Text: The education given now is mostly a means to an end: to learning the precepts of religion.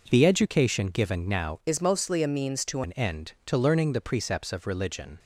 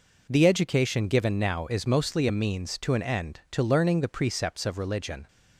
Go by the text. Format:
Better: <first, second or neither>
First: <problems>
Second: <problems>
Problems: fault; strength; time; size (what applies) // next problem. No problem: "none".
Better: second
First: changes voice from "is" to "to"; from 1.6 to 2.8 s; 1.2 s long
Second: none